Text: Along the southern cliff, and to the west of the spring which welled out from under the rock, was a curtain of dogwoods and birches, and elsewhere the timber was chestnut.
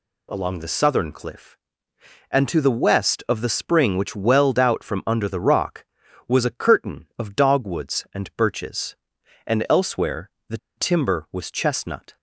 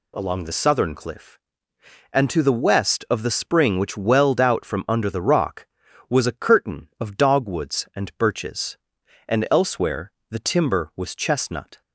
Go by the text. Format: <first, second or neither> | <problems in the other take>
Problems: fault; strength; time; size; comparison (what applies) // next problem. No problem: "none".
second | pauses between "elsewhere" and "the"; slight; at 10.2 s; 0.18 s long; slight in the second // pauses between "the" and "timber"; slight; at 10.5 s; 0.19 s long